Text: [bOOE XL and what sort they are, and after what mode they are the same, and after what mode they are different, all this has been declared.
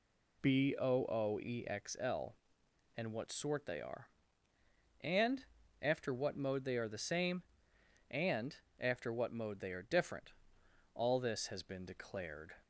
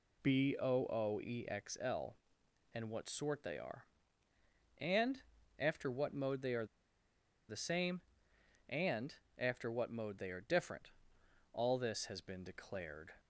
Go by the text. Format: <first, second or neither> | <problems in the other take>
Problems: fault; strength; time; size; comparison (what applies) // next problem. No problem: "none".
first | pauses between "and" and "after"; slight; at 5.2 s; 0.36 s long; slight in the first // pauses between "are" and "the"; noticeable; at 6.6 s; 0.84 s long // pauses between "and" and "after"; slight; at 9.1 s; 0.22 s long; slight in the first